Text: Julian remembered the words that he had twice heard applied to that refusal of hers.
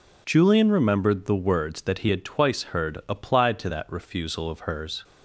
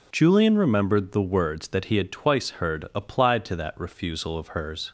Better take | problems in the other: neither | none

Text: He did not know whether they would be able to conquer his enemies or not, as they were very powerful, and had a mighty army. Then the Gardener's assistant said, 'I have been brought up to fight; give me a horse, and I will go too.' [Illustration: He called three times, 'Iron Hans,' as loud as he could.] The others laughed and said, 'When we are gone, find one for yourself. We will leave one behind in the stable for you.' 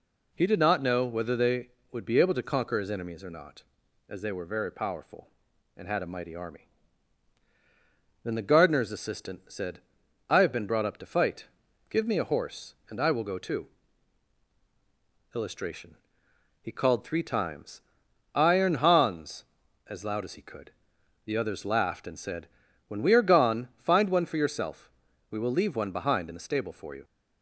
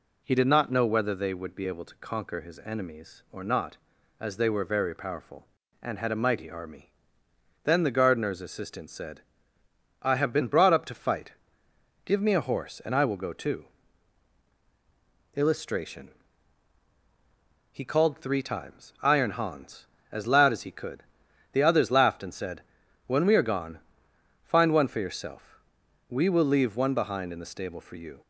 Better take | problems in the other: neither | none

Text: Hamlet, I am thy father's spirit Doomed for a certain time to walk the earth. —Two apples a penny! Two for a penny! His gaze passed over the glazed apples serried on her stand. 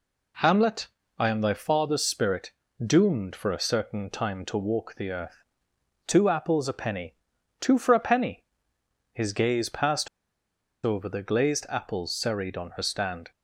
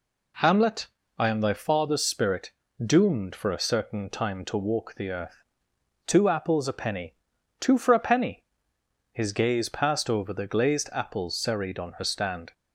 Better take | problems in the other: second | pauses between "spirit" and "Doomed"; slight; at 2.5 s; 0.34 s long; slight in the second // pauses between "passed" and "over"; noticeable; at 10.0 s; 0.76 s long

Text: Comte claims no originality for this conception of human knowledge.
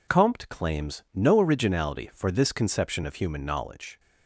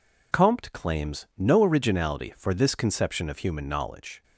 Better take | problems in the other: neither | none

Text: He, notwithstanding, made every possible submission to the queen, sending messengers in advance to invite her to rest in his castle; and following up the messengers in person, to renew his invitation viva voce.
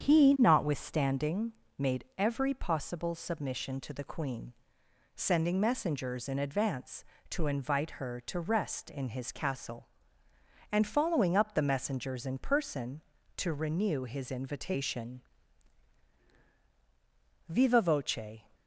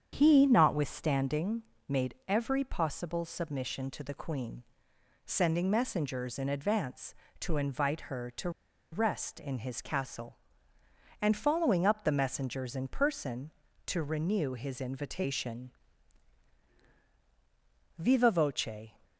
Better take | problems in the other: first | starts louder than the rest; strong; until 1.1 s; 8 dB; strong in the first // pauses between "to" and "rest"; at 8.4 s; 0.42 s long // pauses between "invitation" and "viva"; strong; at 15.7 s; 2.2 s long; strong in the first

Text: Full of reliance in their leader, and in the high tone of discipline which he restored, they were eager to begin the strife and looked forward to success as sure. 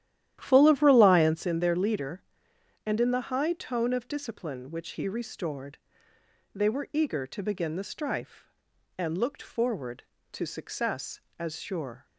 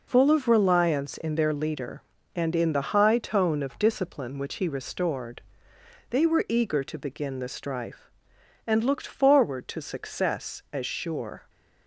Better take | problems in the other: second | starts louder than the rest; strong; until 1.5 s; 12 dB

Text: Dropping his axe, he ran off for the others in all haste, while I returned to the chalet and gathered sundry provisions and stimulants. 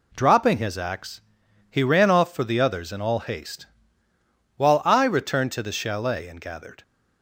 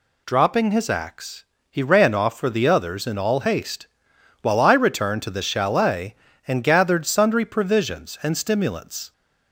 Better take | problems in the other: second | stops before "sundry provisions and stimulants"; at 6.8 s

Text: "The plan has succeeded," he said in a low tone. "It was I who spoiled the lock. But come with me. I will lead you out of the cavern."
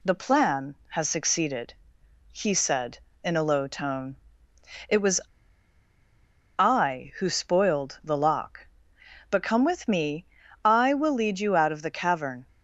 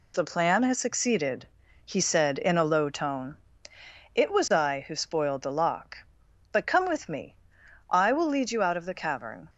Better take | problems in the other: second | pauses between "was" and "I"; strong; at 5.1 s; 1.3 s long

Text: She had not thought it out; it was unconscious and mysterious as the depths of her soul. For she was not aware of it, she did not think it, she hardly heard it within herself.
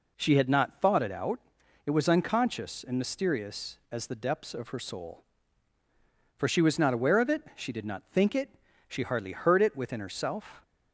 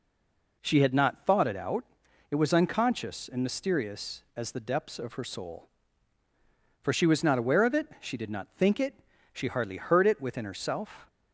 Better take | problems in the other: first | stays silent before the first word; slight; until 0.6 s; 0.6 s long

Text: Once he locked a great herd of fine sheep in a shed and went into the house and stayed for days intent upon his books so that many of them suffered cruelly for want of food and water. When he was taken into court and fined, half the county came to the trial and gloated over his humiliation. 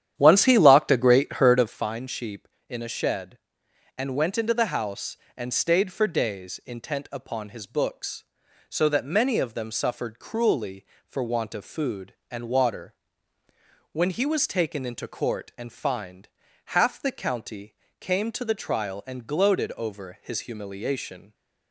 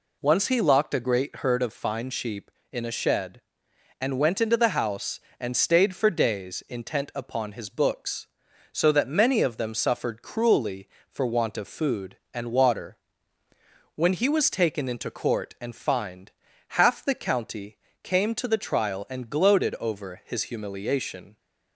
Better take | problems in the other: second | starts louder than the rest; strong; until 1.9 s; 10 dB // pauses between "county" and "came"; slight; at 17.7 s; 0.26 s long; slight in the second

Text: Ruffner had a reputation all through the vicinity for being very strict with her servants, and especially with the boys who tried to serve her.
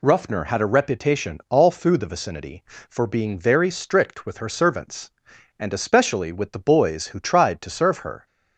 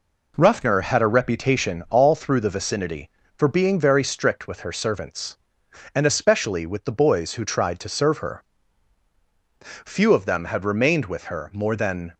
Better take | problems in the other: first | goes on to say "Few of them had remained with her more than"; strong; from 9.6 s on; 2.5 s long

